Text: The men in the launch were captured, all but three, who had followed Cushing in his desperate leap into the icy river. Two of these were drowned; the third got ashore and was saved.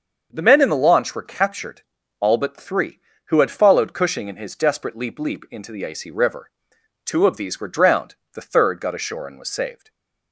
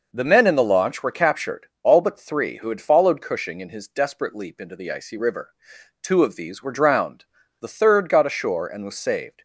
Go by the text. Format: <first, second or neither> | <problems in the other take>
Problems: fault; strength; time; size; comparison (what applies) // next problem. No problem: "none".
second | starts louder than the rest; until 1.3 s; 6.5 dB // says "leap" twice; at 5.1 s // stays silent after the last word; slight; from 9.7 s on; 0.6 s long